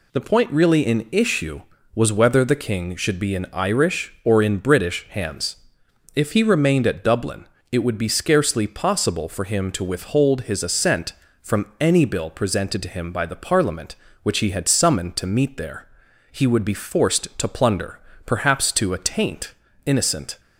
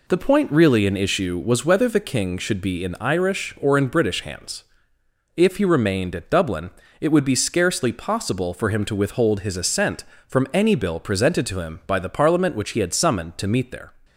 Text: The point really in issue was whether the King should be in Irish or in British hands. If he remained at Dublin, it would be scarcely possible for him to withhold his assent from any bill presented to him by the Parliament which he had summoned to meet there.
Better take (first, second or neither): second